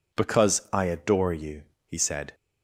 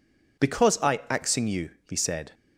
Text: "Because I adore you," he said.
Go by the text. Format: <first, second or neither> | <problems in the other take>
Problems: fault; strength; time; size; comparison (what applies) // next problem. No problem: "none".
first | says "axing" for "adore"; at 1.0 s